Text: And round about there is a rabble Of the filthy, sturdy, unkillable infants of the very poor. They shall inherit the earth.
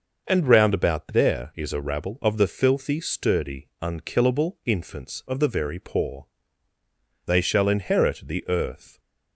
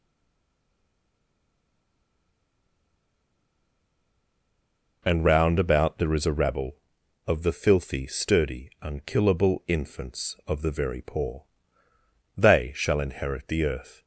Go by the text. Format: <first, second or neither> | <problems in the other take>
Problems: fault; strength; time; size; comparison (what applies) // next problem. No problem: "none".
first | stays silent before the first word; strong; until 5.0 s; 5.0 s long